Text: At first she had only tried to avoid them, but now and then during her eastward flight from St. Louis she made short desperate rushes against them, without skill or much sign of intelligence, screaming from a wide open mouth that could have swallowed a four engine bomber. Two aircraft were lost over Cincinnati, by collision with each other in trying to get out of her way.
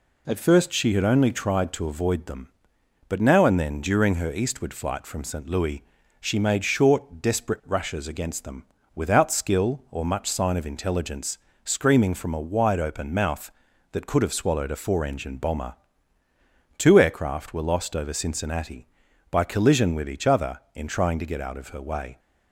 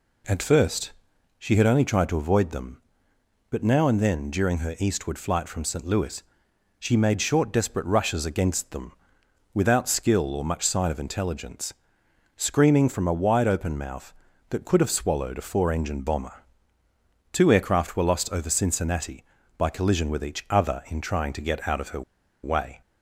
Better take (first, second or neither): first